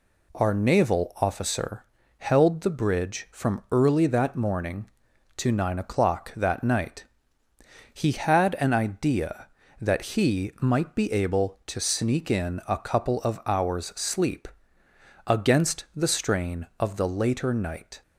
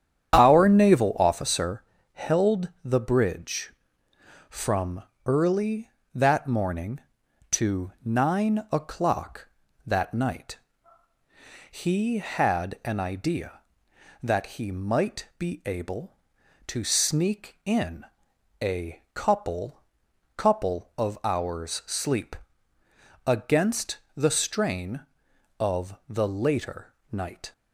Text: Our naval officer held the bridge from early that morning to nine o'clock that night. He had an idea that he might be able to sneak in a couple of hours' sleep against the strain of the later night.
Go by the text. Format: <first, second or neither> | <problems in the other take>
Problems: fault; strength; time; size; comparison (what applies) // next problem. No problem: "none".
first | starts louder than the rest; strong; until 1.3 s; 9 dB // pauses between "officer" and "held"; slight; at 1.8 s; 0.30 s long; slight in the first // pauses between "from" and "early"; slight; at 5.0 s; 0.24 s long // pauses between "in" and "a"; noticeable; at 18.0 s; 0.56 s long // says "couple" twice; at 20.3 s // pauses between "sleep" and "against"; noticeable; at 22.3 s; 0.90 s long; noticeable in the first // pauses between "against" and "the"; slight; at 23.9 s; 0.18 s long // pauses between "later" and "night"; slight; at 26.9 s; 0.20 s long